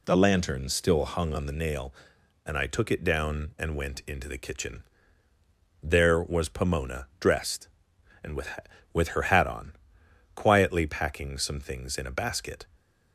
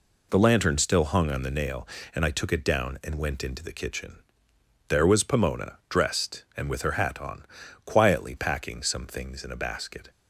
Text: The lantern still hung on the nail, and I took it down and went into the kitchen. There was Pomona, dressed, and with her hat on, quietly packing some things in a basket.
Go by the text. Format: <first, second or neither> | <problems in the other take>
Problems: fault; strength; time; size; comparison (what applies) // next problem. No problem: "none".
second | says "with" twice; at 8.9 s